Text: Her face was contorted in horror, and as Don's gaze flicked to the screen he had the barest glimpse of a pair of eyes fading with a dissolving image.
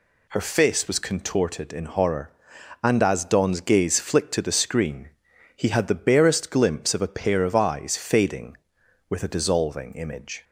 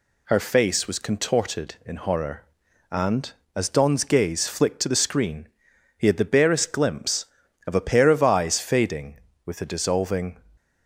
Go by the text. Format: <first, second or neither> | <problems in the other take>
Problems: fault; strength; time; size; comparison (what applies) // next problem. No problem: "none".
first | pauses between "screen" and "he"; noticeable; at 5.4 s; 0.48 s long; noticeable in the first // stops before "image"; at 10.5 s